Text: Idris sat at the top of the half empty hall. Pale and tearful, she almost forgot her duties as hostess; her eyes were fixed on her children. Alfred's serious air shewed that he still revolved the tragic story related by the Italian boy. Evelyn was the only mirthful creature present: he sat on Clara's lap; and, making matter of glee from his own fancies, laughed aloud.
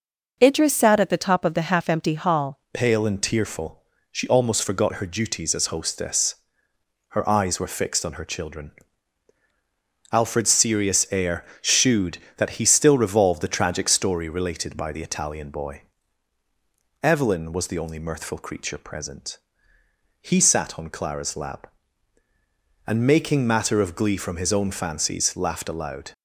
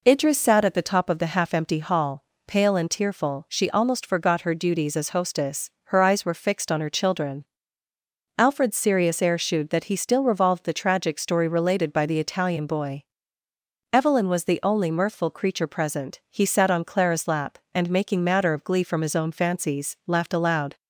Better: second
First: changes voice at "Pale"; from 2.7 s on; 23.4 s long // pauses between "air" and "shewed"; slight; at 11.4 s; 0.16 s long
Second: none

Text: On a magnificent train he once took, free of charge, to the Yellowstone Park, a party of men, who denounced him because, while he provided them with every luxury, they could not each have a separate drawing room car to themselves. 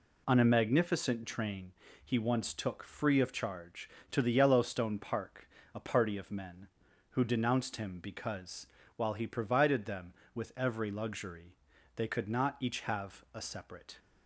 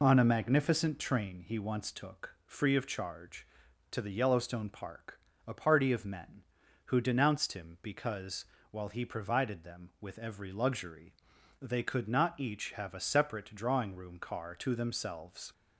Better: second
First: pauses between "train" and "he"; slight; at 1.7 s; 0.30 s long // stops before "drawing room car to themselves"; at 13.9 s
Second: none

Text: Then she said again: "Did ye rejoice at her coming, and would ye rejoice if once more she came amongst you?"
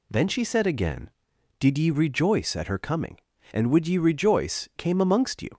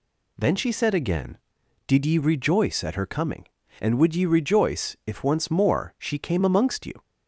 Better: second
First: skips "if once more she"; at 4.7 s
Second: none

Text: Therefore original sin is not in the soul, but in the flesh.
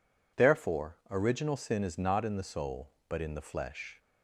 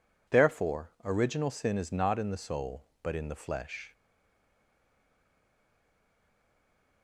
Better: first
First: none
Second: stays silent after the last word; strong; from 3.9 s on; 3.1 s long

